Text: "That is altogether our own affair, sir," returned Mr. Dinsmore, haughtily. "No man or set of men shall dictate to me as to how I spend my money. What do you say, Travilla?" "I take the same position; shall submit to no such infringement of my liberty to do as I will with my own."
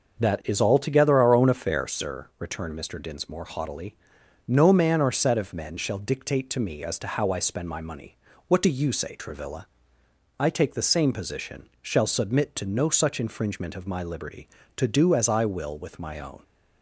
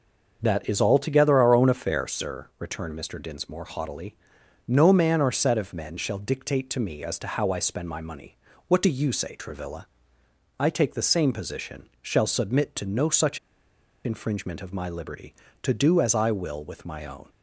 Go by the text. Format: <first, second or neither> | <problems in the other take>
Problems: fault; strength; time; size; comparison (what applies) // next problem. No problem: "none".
first | starts louder than the rest; until 1.4 s; 6 dB; also in the first // pauses between "such" and "infringement"; noticeable; at 13.3 s; 0.66 s long